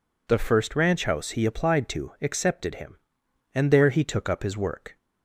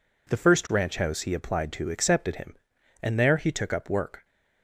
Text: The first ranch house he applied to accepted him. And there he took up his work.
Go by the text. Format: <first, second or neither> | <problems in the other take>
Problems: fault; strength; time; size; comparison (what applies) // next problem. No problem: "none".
first | skips "his"; at 3.9 s